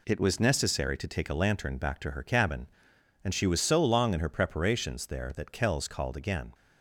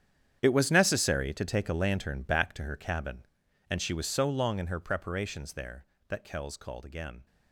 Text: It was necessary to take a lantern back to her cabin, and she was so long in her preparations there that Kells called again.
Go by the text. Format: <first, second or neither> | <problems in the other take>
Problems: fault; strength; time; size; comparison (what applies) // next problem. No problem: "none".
first | gets quieter; strong; throughout; 16.5 dB